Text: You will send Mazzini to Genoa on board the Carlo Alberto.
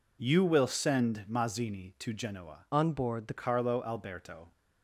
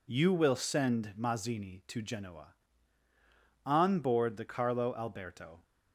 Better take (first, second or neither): second